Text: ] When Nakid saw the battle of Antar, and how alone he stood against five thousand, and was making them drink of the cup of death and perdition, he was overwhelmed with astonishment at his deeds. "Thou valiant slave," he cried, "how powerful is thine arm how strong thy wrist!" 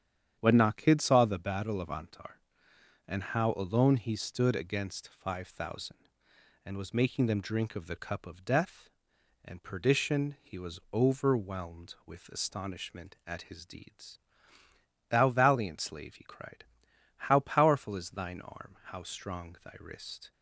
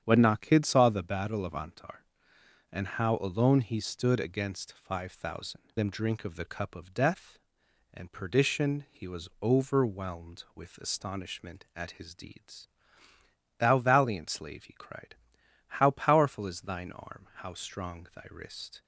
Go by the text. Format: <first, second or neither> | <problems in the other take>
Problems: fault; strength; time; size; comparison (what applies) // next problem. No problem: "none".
first | starts louder than the rest; strong; until 1.0 s; 9 dB; strong in the first // skips "and was making"; at 5.7 s